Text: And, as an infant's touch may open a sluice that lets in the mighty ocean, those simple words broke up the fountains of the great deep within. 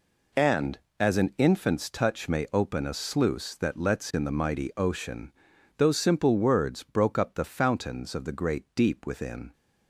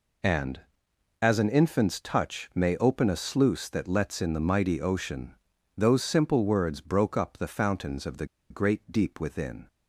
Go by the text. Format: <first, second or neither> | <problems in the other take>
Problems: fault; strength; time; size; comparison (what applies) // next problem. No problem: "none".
first | pauses between "the" and "great"; slight; at 8.2 s; 0.23 s long